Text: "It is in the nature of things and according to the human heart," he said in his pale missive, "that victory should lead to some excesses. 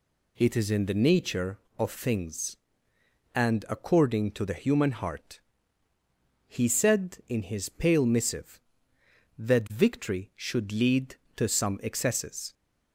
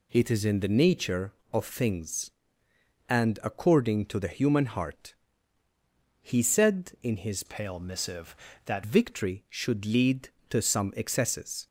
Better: first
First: none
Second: changes voice from "pale" to "that"; from 7.4 to 8.8 s; 1.4 s long

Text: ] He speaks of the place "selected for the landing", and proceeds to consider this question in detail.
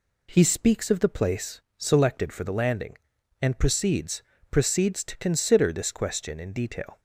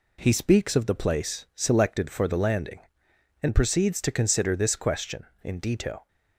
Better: second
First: pauses between "place" and "selected"; slight; at 1.5 s; 0.18 s long // says "proceeds" twice; at 4.5 s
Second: none

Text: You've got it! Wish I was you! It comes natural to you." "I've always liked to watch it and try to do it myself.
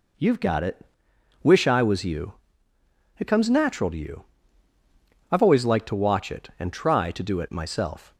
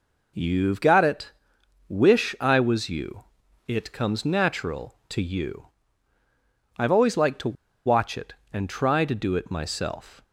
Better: first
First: none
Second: pauses between "to" and "watch"; slight; at 7.5 s; 0.33 s long

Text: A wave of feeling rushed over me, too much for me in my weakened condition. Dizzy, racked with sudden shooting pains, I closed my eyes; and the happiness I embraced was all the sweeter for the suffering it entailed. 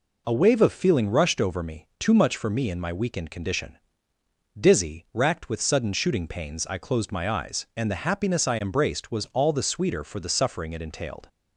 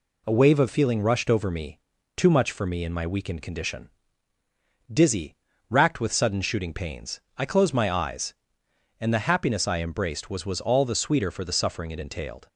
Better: first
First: none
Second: says "was" twice; at 10.4 s

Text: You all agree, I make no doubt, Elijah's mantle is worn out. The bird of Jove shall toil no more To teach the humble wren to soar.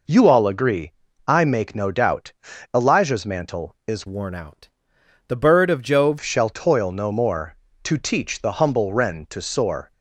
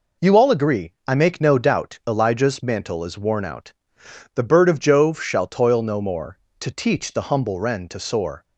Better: second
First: changes voice from "worn" to "Jove"; from 4.0 to 6.1 s; 2.1 s long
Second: none

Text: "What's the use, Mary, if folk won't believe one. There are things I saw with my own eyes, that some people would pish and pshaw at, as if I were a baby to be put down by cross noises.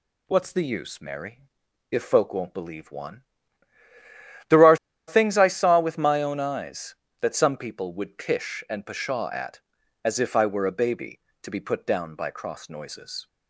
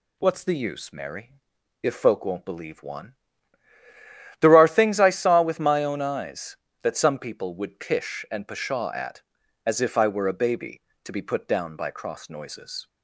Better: second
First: pauses between "are" and "things"; slight; at 4.7 s; 0.32 s long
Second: none

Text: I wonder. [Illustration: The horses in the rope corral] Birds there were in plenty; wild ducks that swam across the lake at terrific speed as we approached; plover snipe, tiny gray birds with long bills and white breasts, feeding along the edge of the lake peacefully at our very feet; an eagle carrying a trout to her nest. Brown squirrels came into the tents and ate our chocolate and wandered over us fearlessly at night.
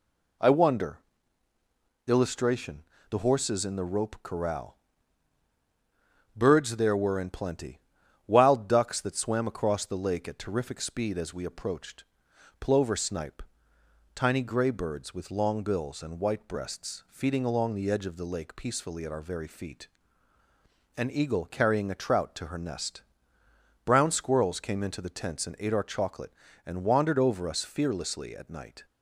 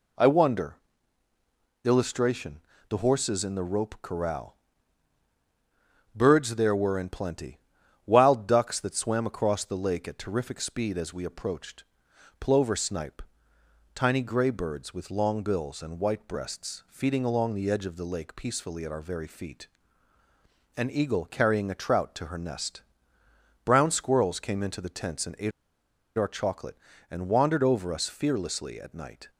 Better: first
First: pauses between "corral" and "Birds"; strong; at 4.7 s; 1.5 s long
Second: pauses between "corral" and "Birds"; strong; at 4.5 s; 1.5 s long // pauses between "ate" and "our"; noticeable; at 25.5 s; 0.67 s long

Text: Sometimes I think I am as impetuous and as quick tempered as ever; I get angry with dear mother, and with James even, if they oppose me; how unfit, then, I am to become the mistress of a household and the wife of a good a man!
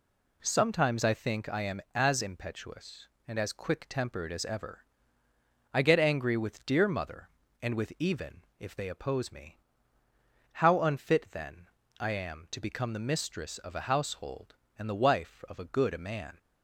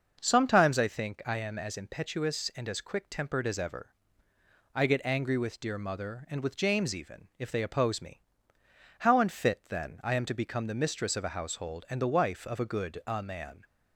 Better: second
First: skips "James"; at 7.9 s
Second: none

